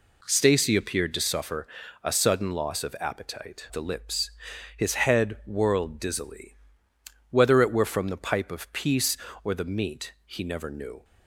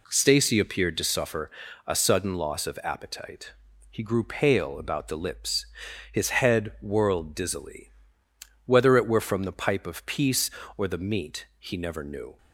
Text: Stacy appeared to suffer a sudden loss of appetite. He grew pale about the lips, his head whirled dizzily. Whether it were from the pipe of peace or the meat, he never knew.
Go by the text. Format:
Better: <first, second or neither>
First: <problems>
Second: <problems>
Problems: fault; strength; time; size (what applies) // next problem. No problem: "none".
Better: second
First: pauses between "suffer" and "a"; at 1.6 s; 0.38 s long // skips "He grew pale about"; at 3.6 s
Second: pauses between "suffer" and "a"; at 1.4 s; 0.38 s long